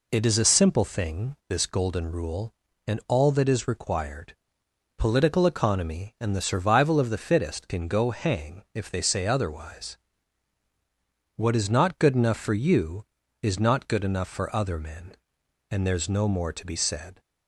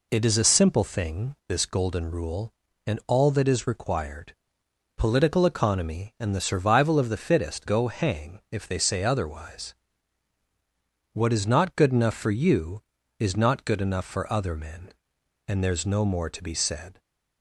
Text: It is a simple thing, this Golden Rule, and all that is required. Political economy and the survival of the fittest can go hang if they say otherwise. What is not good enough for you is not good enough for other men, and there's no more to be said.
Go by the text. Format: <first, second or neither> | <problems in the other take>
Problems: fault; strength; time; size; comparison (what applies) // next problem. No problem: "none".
first | skips "can"; at 7.6 s